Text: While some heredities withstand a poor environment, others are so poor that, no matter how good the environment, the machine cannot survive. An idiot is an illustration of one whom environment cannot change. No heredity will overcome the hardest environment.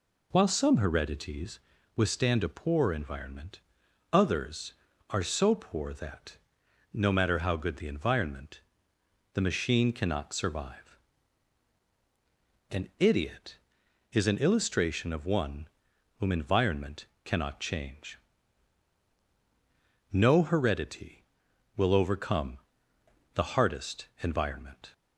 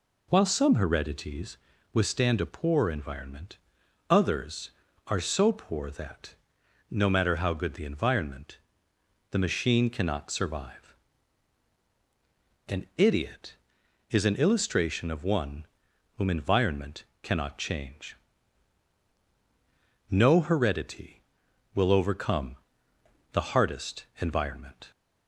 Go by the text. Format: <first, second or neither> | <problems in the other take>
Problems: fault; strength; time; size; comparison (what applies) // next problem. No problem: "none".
neither | pauses between "heredities" and "withstand"; slight; the same in both // pauses between "one" and "whom"; noticeable; the same in both // pauses between "environment" and "cannot"; slight; the same in both // pauses between "overcome" and "the"; noticeable; the same in both // pauses between "hardest" and "environment"; slight; the same in both